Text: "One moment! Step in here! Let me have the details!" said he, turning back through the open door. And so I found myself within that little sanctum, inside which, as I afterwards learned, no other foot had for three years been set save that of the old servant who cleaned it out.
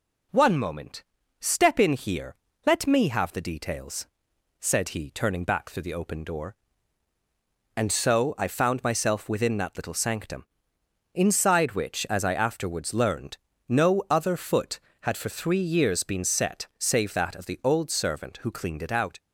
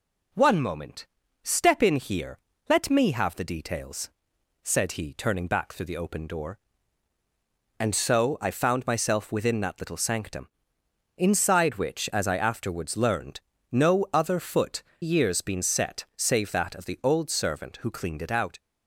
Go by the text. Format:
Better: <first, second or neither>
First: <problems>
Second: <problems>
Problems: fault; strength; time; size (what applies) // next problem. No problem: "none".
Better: first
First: none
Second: skips "had for three"; at 14.9 s